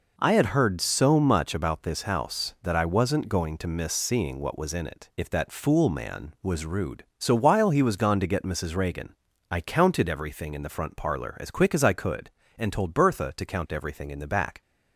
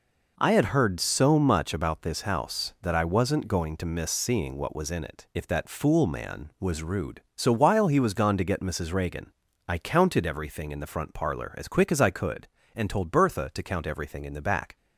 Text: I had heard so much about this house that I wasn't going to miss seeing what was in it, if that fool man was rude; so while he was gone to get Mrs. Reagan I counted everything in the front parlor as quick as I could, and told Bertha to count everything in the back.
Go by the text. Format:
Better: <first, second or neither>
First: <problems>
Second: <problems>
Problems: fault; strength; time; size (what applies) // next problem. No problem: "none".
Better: neither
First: pauses between "Reagan" and "I"; slight; at 9.1 s; 0.36 s long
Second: pauses between "Reagan" and "I"; slight; at 9.3 s; 0.36 s long